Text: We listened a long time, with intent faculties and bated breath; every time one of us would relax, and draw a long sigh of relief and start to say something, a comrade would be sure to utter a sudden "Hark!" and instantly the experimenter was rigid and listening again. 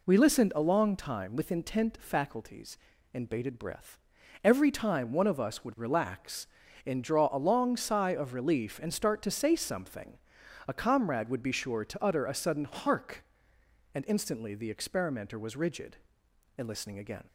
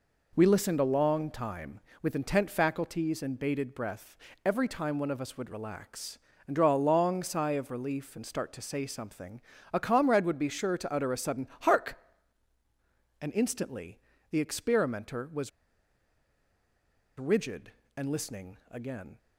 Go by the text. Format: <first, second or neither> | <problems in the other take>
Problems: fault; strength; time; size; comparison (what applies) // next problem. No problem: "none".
first | pauses between "instantly" and "the"; slight; at 13.9 s; 0.32 s long // pauses between "was" and "rigid"; strong; at 15.4 s; 1.6 s long